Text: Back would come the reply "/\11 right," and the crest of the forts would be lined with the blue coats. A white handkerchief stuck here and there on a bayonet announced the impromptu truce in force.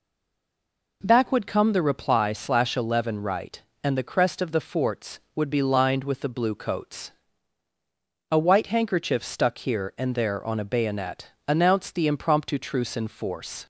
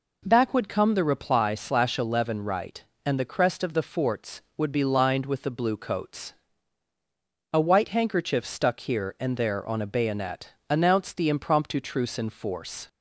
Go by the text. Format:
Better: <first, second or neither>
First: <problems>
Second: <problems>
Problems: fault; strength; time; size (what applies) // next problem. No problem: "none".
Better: second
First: stays silent before the first word; until 1.0 s; 1.0 s long // pauses between "bayonet" and "announced"; slight; at 11.3 s; 0.16 s long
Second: pauses between "bayonet" and "announced"; slight; at 10.5 s; 0.16 s long